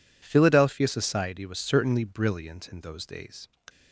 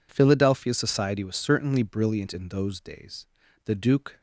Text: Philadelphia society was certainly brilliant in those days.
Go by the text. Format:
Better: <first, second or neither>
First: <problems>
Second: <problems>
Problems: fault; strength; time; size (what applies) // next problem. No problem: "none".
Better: first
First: none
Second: goes on to say "The Duke"; from 3.6 s on; 0.54 s long